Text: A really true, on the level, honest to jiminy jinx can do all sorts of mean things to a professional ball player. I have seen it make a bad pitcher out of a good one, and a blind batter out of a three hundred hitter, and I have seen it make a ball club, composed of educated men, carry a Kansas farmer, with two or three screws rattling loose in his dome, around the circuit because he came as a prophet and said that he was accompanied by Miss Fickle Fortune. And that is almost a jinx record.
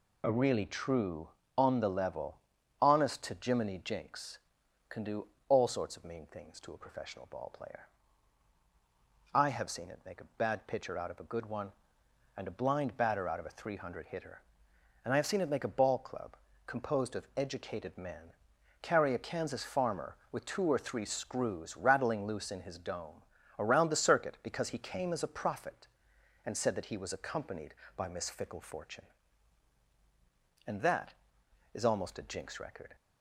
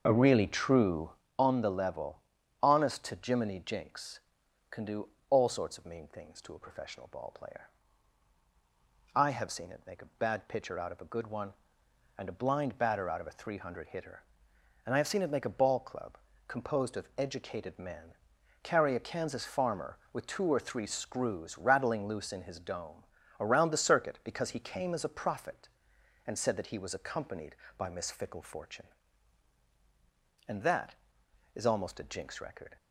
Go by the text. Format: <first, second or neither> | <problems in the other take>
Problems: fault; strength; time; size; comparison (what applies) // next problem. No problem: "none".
first | starts louder than the rest; noticeable; until 1.2 s; 6 dB // pauses between "do" and "all"; slight; at 5.0 s; 0.22 s long; slight in the first